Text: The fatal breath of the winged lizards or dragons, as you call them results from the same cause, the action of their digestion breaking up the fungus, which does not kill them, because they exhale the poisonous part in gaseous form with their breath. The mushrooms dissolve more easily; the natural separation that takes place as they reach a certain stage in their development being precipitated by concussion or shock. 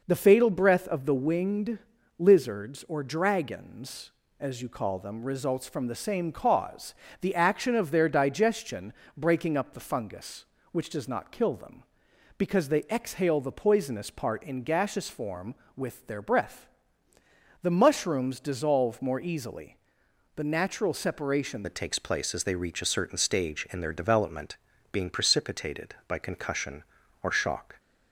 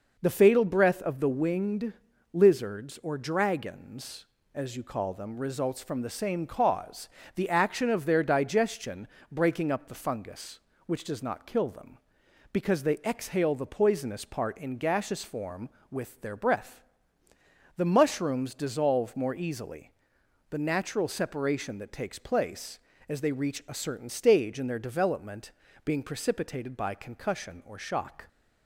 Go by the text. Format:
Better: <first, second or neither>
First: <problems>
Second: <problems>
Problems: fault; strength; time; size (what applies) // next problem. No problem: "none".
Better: second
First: pauses between "winged" and "lizards"; at 1.7 s; 0.40 s long // pauses between "digestion" and "breaking"; slight; at 8.9 s; 0.26 s long // changes voice at "that"; from 21.6 s on; 6.1 s long // pauses between "development" and "being"; slight; at 24.5 s; 0.36 s long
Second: pauses between "winged" and "lizards"; at 1.9 s; 0.40 s long // pauses between "digestion" and "breaking"; slight; at 9.0 s; 0.26 s long // pauses between "development" and "being"; slight; at 25.5 s; 0.32 s long